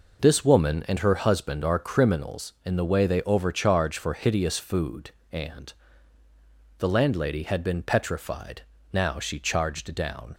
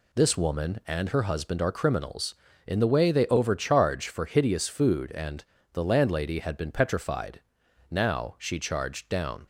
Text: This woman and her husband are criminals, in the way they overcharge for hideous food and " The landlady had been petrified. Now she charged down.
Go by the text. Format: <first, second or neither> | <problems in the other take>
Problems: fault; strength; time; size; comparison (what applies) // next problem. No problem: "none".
neither | none